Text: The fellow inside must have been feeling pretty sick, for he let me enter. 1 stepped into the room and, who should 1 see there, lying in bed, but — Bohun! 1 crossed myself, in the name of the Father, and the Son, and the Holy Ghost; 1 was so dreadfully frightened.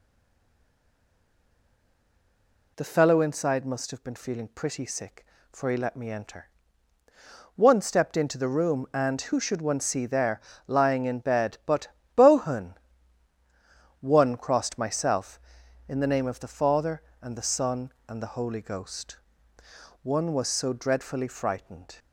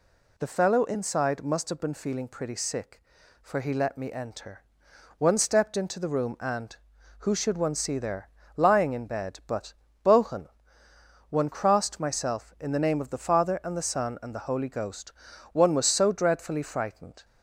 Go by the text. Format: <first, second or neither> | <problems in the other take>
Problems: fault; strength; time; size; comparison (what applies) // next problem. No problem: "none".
second | stays silent before the first word; strong; until 2.7 s; 2.7 s long